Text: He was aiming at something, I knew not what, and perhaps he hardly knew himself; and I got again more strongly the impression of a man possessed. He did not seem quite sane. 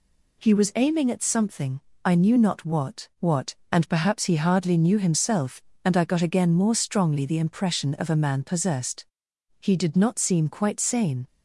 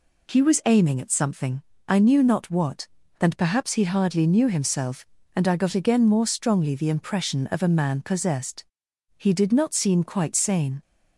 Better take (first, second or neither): second